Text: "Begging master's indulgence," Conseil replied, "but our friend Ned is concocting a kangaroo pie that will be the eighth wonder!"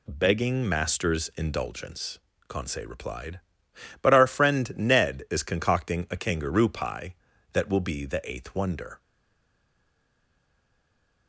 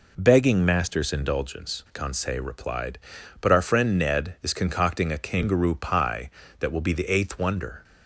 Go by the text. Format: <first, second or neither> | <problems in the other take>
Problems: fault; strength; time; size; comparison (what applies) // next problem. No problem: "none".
second | stays silent after the last word; from 9.0 s on; 2.2 s long